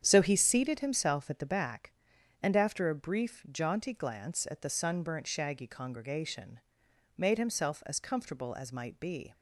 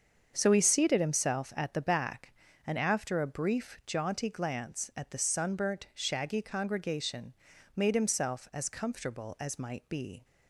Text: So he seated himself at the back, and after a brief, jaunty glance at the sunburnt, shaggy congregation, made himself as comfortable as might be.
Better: neither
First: starts louder than the rest; strong; until 1.0 s; 8.5 dB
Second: starts louder than the rest; until 1.3 s; 7 dB

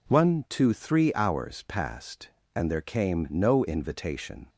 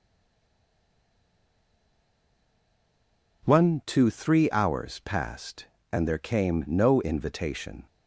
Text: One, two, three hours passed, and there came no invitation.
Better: first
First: none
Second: stays silent before the first word; strong; until 3.4 s; 3.4 s long

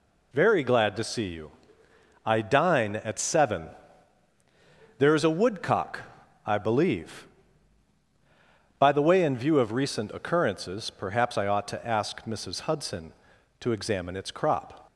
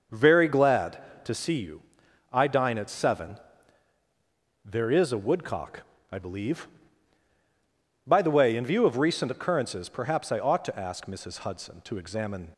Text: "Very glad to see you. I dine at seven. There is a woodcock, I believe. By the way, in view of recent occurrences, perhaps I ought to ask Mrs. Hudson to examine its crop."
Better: first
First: none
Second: starts louder than the rest; noticeable; until 1.3 s; 6 dB // stops before "its crop"; at 12.5 s

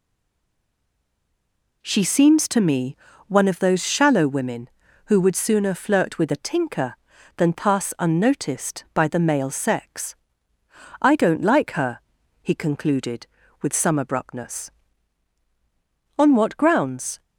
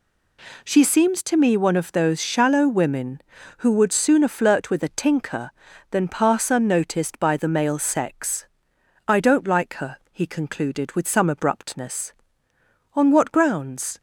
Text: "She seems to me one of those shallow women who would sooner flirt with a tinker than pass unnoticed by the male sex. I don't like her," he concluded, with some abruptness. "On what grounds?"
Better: second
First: stays silent before the first word; noticeable; until 1.8 s; 1.8 s long // pauses between "me" and "one"; slight; at 2.9 s; 0.30 s long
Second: none

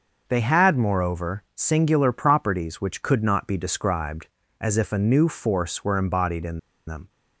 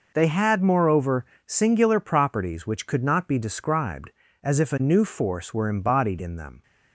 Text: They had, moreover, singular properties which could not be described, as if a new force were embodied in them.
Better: second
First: starts louder than the rest; noticeable; until 1.2 s; 6 dB // pauses between "in" and "them"; slight; at 6.5 s; 0.27 s long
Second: none

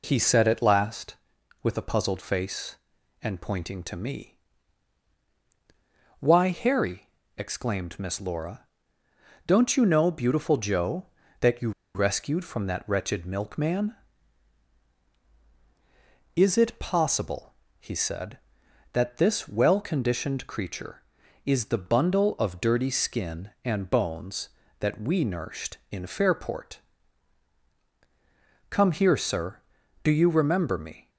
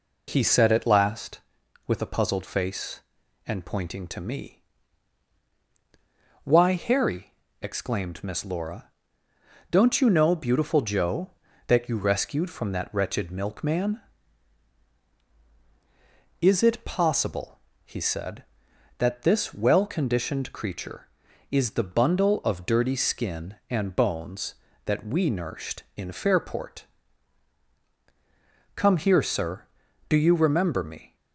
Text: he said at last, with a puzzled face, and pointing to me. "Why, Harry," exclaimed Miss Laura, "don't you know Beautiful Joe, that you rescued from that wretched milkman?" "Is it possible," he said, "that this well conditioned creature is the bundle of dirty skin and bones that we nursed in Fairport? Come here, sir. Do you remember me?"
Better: second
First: pauses between "you" and "rescued"; slight; at 11.7 s; 0.24 s long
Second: none

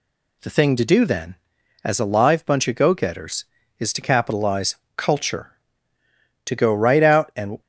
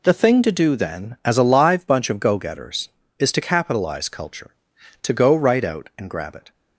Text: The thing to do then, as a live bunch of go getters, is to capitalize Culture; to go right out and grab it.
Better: second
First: pauses between "capitalize" and "Culture"; slight; at 4.7 s; 0.18 s long // stops before "grab it"; at 7.6 s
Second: none

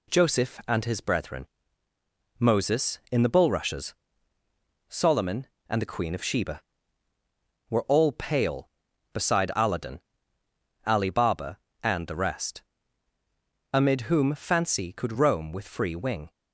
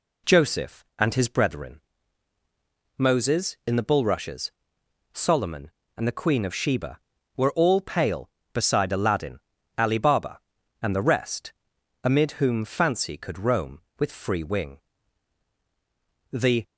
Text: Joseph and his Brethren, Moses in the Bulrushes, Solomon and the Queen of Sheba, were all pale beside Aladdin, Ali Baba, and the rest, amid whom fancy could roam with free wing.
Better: first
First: none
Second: goes on to say "The"; slight; from 16.3 s on; 0.32 s long

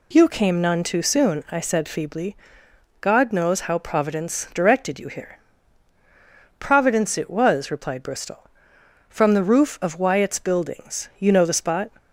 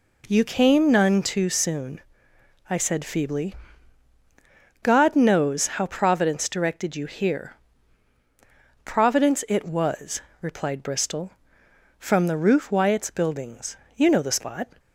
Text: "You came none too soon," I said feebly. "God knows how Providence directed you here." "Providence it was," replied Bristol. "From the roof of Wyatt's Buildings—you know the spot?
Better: first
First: none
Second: skips "of"; at 12.7 s

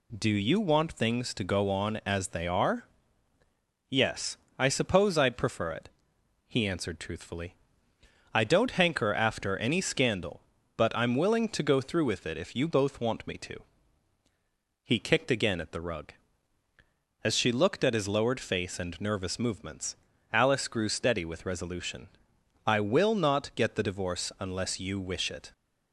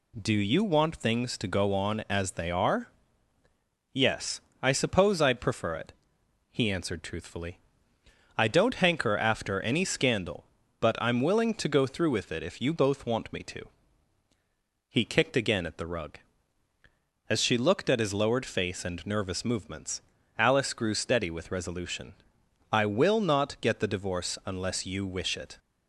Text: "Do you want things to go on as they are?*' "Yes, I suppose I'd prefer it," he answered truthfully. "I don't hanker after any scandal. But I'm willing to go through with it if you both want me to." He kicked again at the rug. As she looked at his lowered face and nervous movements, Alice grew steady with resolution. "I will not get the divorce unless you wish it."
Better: neither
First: none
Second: none

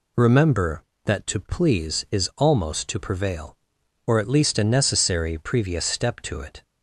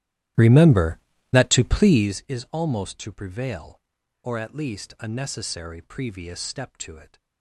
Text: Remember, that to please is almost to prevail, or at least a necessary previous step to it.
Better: first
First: none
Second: starts louder than the rest; strong; until 2.2 s; 13.5 dB

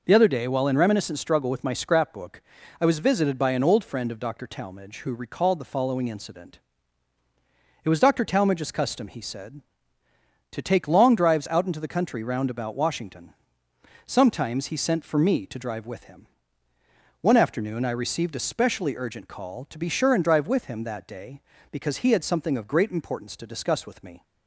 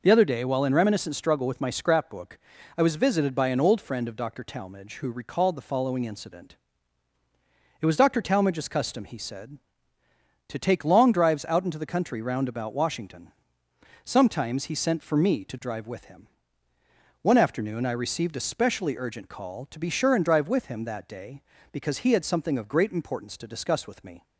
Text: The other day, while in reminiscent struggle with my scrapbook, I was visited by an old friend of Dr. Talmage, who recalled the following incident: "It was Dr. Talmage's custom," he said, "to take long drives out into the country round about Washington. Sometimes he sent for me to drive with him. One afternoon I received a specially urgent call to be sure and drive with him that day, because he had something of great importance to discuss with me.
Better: neither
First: none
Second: none

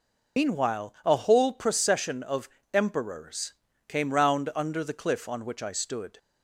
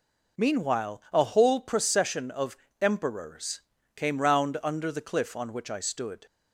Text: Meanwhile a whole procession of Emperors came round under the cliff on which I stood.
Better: second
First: loses the start of "Meanwhile"; at 0.3 s; 65 ms // pauses between "of" and "Emperors"; slight; at 2.4 s; 0.24 s long // pauses between "Emperors" and "came"; slight; at 3.5 s; 0.36 s long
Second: pauses between "of" and "Emperors"; slight; at 2.5 s; 0.24 s long // pauses between "Emperors" and "came"; slight; at 3.5 s; 0.36 s long

